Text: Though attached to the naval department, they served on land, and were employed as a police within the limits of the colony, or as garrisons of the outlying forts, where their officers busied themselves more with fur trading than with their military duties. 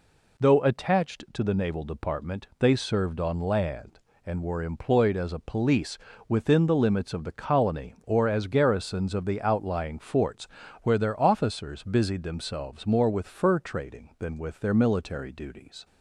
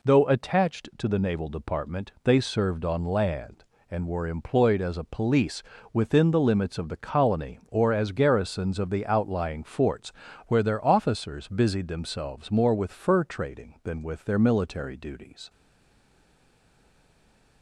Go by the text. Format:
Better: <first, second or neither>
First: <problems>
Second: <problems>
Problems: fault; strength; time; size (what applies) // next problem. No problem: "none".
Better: first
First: pauses between "police" and "within"; slight; at 5.9 s; 0.30 s long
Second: pauses between "police" and "within"; slight; at 5.6 s; 0.30 s long // stays silent after the last word; from 15.4 s on; 2.2 s long